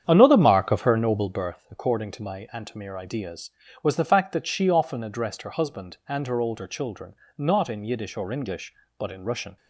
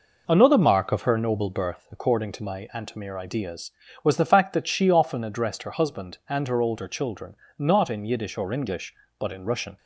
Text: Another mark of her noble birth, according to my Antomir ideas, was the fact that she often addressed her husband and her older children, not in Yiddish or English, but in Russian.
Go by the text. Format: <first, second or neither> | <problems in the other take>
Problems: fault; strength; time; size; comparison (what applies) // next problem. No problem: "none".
second | starts louder than the rest; strong; until 1.4 s; 8.5 dB